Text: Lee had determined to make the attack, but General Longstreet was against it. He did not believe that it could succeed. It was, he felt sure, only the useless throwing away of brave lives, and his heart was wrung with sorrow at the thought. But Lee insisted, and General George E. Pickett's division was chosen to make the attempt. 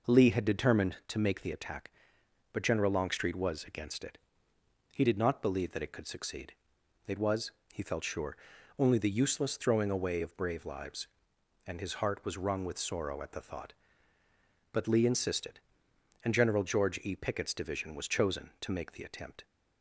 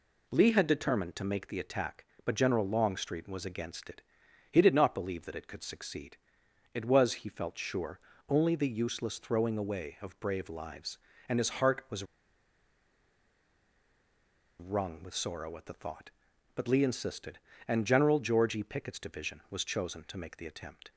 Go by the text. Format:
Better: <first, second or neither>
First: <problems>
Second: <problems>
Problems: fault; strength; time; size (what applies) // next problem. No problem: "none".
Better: first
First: none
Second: pauses between "was" and "wrung"; strong; at 12.0 s; 2.5 s long